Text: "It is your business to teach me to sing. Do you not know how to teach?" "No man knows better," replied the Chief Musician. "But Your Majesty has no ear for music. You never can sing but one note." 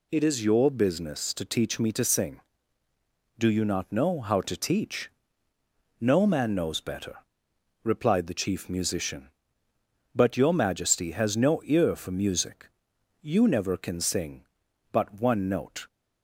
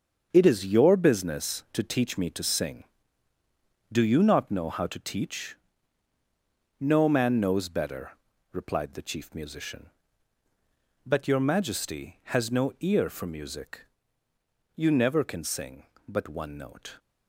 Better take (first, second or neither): first